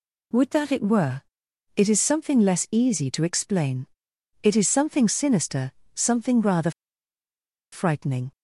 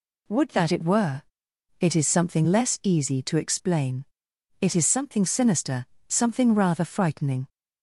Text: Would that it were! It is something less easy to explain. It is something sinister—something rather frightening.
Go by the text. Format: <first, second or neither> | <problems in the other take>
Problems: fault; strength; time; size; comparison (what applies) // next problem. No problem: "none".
second | pauses between "rather" and "frightening"; at 6.6 s; 1.0 s long